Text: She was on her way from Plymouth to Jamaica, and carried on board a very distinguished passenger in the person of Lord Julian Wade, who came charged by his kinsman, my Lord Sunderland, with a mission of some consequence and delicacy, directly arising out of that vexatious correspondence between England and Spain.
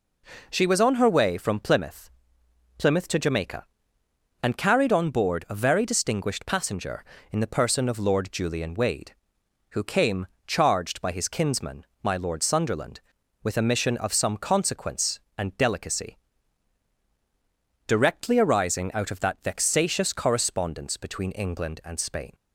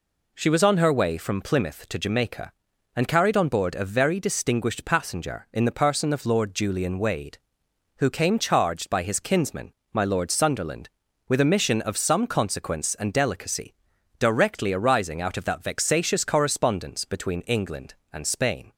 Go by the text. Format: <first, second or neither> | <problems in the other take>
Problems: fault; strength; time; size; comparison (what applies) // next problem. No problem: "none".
second | says "Plymouth" twice; at 2.7 s // pauses between "came" and "charged"; slight; at 10.2 s; 0.20 s long